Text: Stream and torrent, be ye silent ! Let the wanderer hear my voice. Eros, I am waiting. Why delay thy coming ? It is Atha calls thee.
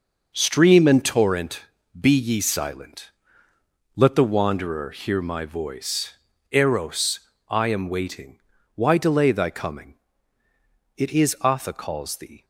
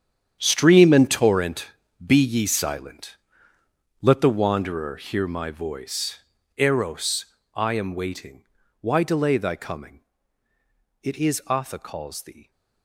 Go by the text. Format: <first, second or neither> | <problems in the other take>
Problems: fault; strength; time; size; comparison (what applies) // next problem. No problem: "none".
first | gets quieter; strong; throughout; 14 dB